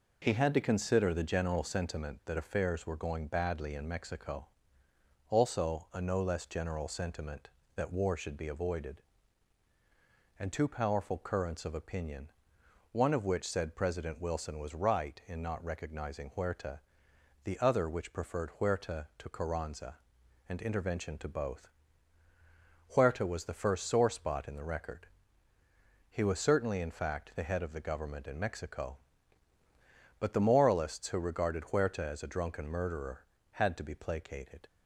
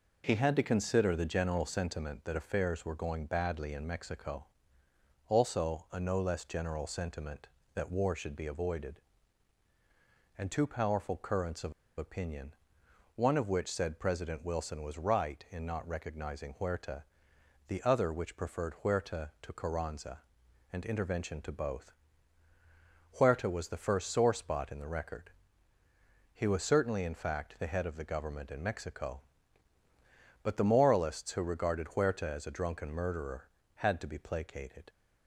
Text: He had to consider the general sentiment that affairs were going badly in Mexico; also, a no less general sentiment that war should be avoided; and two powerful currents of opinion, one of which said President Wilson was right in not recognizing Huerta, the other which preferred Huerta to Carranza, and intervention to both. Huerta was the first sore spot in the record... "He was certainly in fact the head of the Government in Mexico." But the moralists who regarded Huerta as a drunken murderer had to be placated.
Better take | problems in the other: first | pauses between "of" and "opinion"; slight; at 11.7 s; 0.27 s long

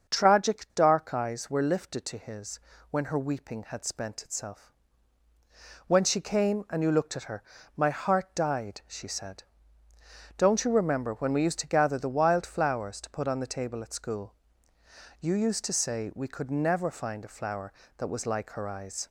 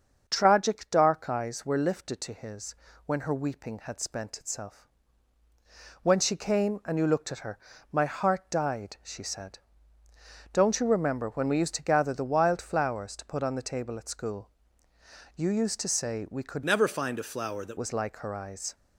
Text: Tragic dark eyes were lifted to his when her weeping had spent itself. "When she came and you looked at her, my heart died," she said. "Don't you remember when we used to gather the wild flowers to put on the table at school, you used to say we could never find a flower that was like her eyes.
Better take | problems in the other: first | starts louder than the rest; until 1.2 s; 6.5 dB; also in the first // pauses between "his" and "when"; slight; at 2.7 s; 0.30 s long; slight in the first // changes voice from "never" to "that"; from 16.6 to 17.7 s; 1.1 s long

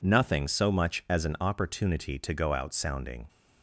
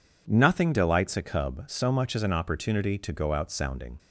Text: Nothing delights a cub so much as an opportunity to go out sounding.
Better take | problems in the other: second | skips "delights a cub"; at 0.4 s

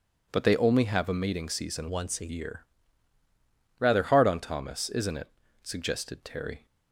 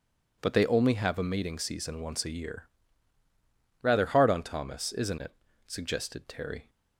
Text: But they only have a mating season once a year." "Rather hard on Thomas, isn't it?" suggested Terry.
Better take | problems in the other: second | changes voice from "once" to "a"; from 1.8 to 2.2 s; 0.4 s long

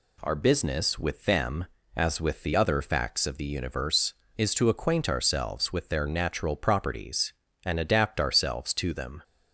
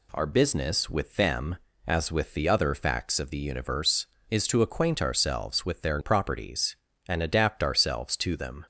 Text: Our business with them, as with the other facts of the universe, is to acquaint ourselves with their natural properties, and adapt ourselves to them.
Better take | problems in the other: first | skips "natural"; at 6.0 s

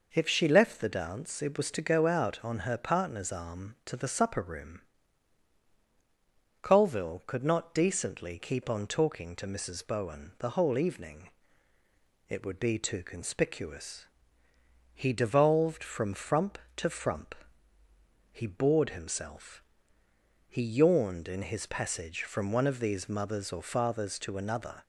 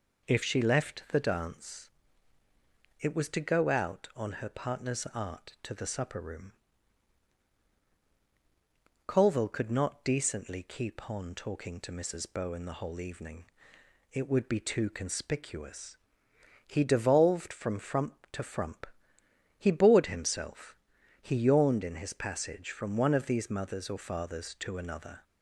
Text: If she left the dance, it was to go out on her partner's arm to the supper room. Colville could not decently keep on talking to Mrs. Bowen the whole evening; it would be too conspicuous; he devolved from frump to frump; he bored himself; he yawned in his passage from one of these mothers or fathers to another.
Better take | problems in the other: first | says "art" for "arm"; at 5.1 s

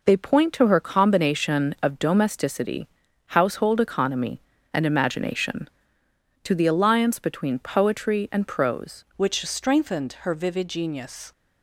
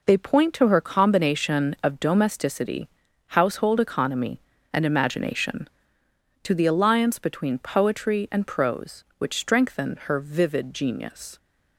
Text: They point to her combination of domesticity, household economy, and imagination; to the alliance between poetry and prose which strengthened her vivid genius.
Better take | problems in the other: second | changes voice at "which"; from 9.1 s on; 2.2 s long

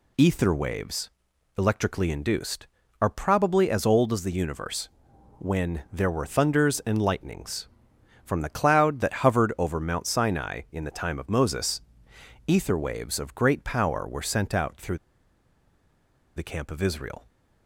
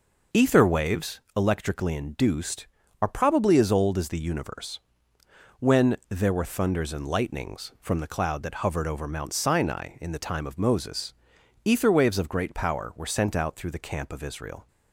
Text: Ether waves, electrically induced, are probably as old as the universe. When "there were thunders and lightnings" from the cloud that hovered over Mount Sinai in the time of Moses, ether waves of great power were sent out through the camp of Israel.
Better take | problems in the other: second | pauses between "through" and "the"; strong; at 14.9 s; 1.3 s long

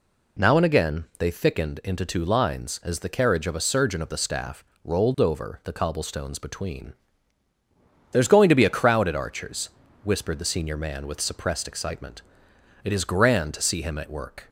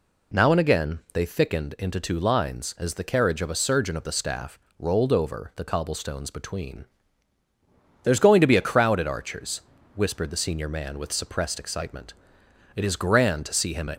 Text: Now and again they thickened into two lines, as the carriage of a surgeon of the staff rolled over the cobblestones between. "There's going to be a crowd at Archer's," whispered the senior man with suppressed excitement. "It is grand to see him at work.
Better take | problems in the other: first | pauses between "staff" and "rolled"; slight; at 4.5 s; 0.20 s long; slight in the first // stops before "work"; at 13.9 s

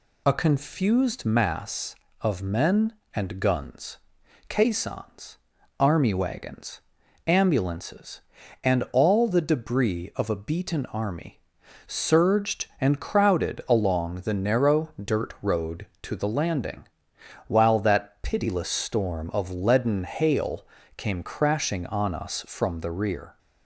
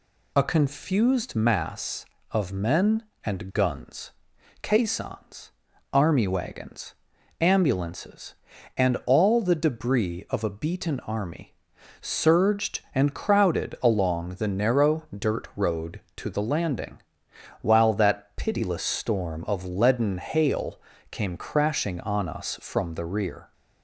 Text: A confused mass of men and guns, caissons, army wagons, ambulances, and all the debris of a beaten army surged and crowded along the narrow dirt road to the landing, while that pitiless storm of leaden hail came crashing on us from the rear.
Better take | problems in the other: neither | pauses between "army" and "surged"; noticeable; the same in both // pauses between "hail" and "came"; slight; the same in both

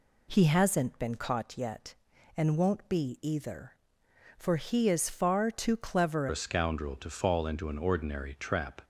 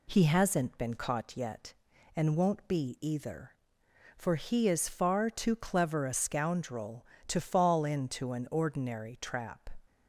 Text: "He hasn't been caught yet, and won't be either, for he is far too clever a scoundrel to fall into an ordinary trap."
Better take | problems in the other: second | changes voice at "a"; from 6.2 s on; 2.6 s long

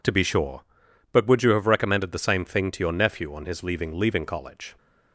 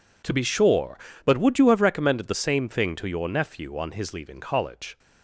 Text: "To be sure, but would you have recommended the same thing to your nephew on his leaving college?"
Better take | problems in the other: second | says "leaving" twice; at 3.9 s

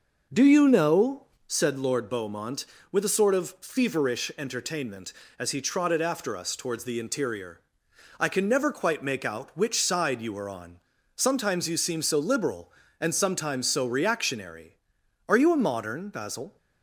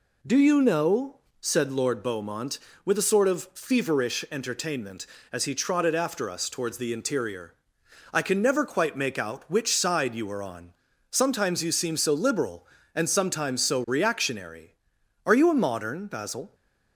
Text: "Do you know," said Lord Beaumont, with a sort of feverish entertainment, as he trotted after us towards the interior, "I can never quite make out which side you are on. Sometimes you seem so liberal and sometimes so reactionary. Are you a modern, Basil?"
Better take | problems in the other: second | starts louder than the rest; noticeable; until 1.7 s; 6 dB

